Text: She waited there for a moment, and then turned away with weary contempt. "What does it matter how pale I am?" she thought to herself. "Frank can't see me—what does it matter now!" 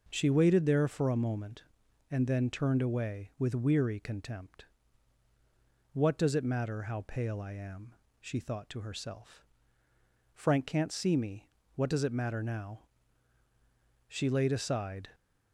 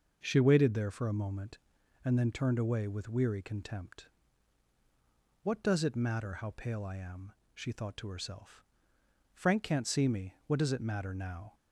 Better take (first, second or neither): second